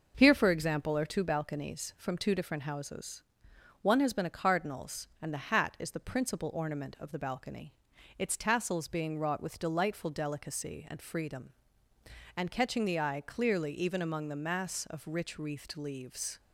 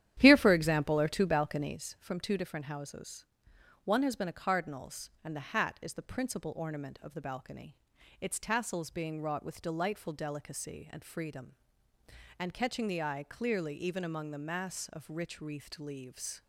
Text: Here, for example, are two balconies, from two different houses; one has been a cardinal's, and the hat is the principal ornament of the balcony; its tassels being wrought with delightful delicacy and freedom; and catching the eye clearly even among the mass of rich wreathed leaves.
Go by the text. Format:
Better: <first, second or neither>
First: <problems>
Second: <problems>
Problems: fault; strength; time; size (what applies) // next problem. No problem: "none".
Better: first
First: none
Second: starts louder than the rest; strong; until 1.8 s; 11 dB